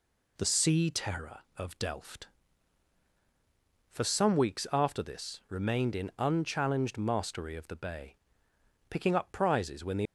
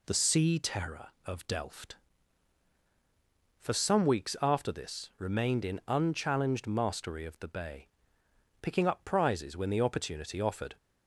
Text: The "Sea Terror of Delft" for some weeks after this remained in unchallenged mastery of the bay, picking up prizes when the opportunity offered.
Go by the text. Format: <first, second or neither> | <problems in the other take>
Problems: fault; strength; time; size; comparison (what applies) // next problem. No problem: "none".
second | stops before "opportunity offered"; at 10.0 s